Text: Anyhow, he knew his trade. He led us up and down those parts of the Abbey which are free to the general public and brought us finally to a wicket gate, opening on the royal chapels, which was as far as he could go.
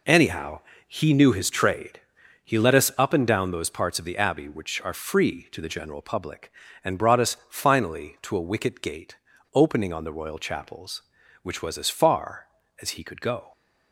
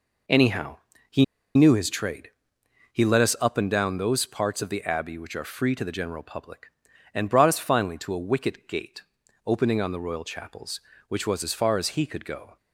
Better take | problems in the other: first | pauses between "he" and "knew"; slight; at 1.2 s; 0.32 s long

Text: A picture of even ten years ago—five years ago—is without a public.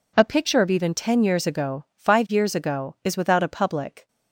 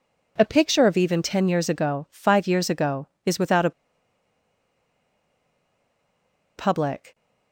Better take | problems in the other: first | pauses between "a" and "public"; strong; at 3.7 s; 2.8 s long

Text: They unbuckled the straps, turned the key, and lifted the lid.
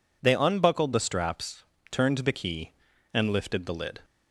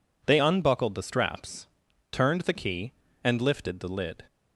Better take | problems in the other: neither | none

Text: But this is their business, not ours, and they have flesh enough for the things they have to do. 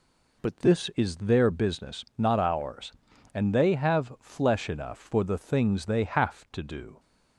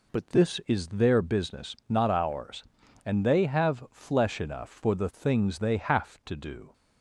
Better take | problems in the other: neither | none

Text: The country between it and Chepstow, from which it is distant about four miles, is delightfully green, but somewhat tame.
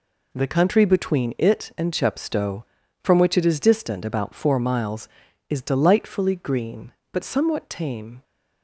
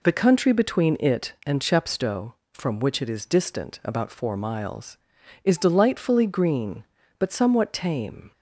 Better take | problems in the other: neither | none

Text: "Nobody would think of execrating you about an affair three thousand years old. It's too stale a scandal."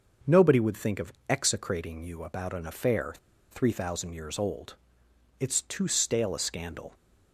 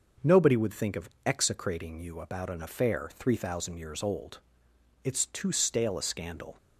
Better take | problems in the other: second | starts louder than the rest; noticeable; until 1.4 s; 6 dB; noticeable in the second // pauses between "of" and "execrating"; slight; at 1.1 s; 0.16 s long; slight in the second // pauses between "affair" and "three"; at 3.1 s; 0.38 s long

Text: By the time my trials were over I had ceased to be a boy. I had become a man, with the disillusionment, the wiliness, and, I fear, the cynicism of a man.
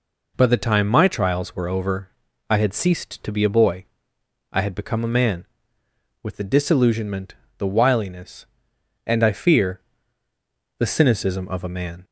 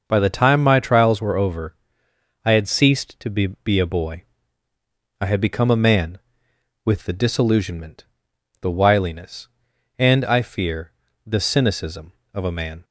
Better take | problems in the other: first | pauses between "over" and "I"; noticeable; at 1.7 s; 0.70 s long; also in the first // says "be" twice; at 3.6 s

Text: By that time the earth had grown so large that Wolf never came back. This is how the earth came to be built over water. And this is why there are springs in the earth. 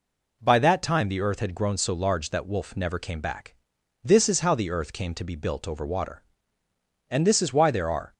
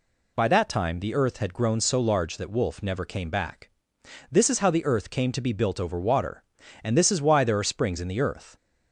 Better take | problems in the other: second | stops before "springs in the earth"; at 8.1 s

